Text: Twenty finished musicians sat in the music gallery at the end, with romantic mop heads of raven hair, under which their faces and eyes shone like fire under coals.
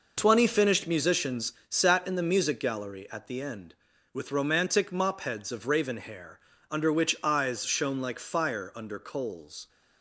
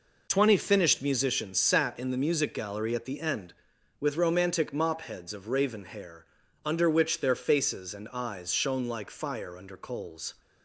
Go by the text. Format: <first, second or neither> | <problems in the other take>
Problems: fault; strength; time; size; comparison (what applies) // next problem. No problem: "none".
second | pauses between "musicians" and "sat"; slight; at 1.5 s; 0.16 s long // skips "their faces and"; at 7.1 s